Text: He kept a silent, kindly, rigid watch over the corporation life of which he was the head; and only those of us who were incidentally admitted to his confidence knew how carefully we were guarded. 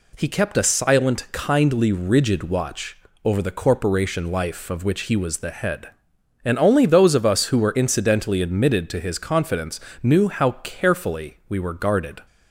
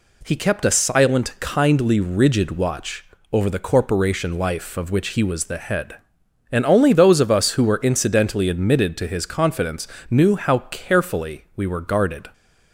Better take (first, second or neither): neither